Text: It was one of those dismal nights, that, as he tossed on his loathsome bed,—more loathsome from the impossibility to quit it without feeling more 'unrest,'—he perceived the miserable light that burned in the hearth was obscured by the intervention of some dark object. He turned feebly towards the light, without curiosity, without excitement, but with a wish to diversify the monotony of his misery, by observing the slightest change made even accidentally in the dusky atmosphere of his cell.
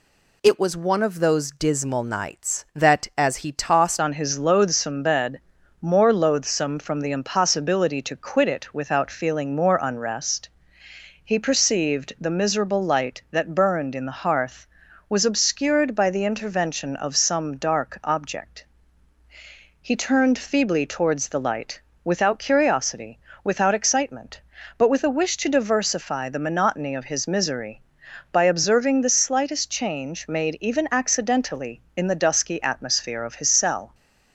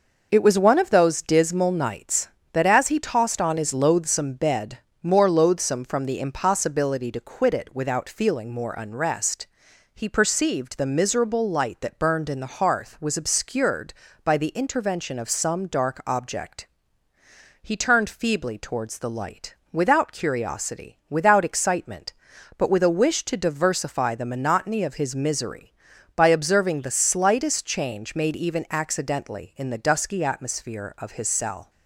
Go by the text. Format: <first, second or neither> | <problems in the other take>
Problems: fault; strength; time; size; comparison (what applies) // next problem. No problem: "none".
second | changes voice at "on"; from 4.0 s on; 29.9 s long